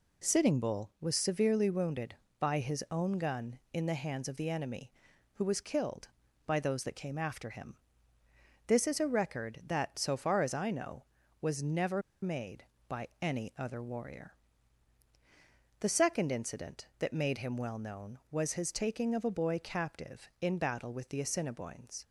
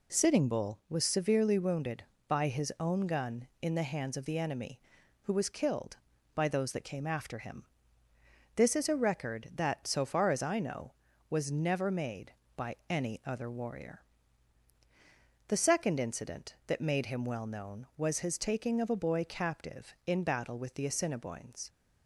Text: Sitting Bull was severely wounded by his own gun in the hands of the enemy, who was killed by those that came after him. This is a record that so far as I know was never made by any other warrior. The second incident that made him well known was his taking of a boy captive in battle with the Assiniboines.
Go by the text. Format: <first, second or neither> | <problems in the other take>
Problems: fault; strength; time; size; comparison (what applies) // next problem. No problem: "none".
second | pauses between "never" and "made"; slight; at 12.0 s; 0.21 s long